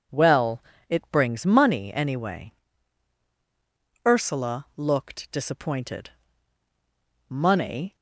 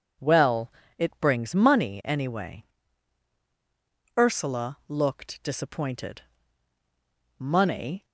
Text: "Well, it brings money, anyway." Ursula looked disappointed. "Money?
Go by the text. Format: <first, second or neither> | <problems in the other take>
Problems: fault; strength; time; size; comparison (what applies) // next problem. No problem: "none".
neither | none